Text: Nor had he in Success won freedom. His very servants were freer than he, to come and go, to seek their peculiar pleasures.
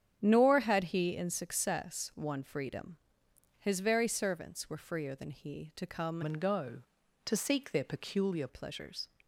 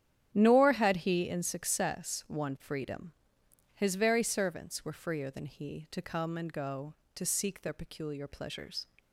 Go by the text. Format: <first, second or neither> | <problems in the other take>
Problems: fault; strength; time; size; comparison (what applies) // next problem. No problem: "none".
second | starts louder than the rest; strong; until 1.2 s; 8.5 dB; strong in the second // changes voice from "and" to "peculiar"; from 6.2 to 8.4 s; 2.2 s long